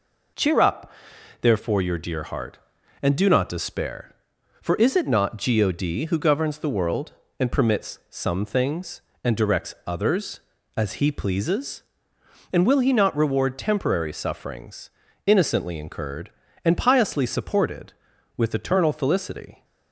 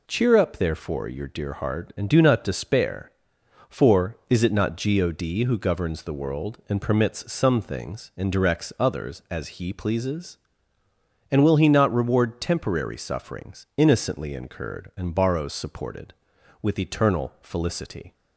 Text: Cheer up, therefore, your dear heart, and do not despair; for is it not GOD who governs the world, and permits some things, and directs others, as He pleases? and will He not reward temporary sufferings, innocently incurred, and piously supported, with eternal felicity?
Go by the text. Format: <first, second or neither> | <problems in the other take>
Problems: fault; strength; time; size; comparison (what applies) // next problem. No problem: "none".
first | says "borrows" for "piously"; at 15.1 s